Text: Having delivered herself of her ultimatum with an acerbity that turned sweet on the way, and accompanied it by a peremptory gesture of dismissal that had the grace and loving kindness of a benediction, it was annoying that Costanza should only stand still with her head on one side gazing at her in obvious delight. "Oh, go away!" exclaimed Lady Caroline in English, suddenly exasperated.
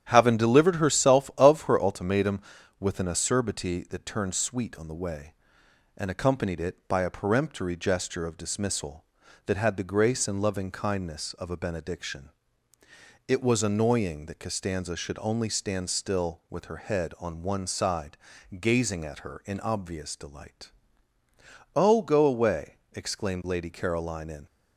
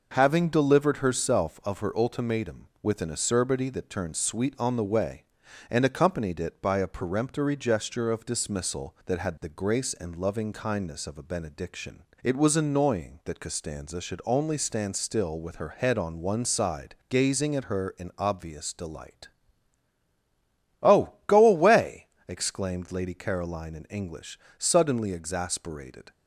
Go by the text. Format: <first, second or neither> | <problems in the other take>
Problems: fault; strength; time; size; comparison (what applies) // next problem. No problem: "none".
second | starts louder than the rest; strong; until 1.0 s; 10 dB // pauses between "side" and "gazing"; at 18.1 s; 0.42 s long; slight in the second // stops before "English suddenly exasperated"; at 24.4 s